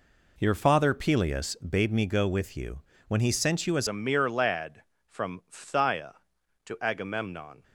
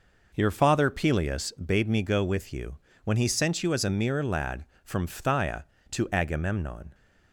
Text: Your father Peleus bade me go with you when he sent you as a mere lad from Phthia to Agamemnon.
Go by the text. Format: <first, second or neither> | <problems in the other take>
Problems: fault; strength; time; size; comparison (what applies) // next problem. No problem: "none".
second | pauses between "you" and "when"; slight; at 2.7 s; 0.28 s long; slight in the second // changes voice at "a"; from 3.8 s on; 3.8 s long